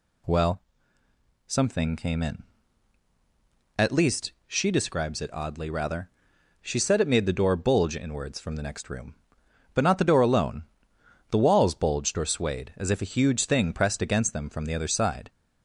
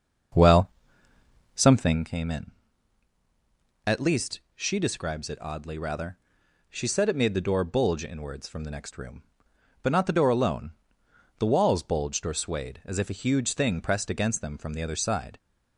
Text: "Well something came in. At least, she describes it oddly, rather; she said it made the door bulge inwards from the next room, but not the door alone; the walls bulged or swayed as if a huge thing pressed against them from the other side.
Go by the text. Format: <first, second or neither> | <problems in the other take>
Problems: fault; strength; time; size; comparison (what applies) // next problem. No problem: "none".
first | starts louder than the rest; until 2.1 s; 6.5 dB // pauses between "Well" and "something"; noticeable; at 0.6 s; 0.88 s long; noticeable in the first